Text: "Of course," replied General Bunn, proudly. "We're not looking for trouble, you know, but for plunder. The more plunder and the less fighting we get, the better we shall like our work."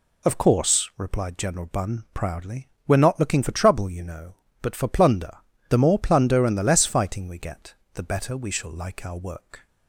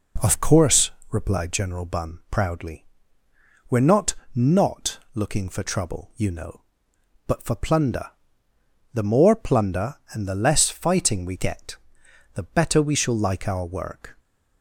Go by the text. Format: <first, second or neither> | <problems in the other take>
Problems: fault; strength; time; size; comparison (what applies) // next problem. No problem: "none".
first | says "not" twice; at 4.3 s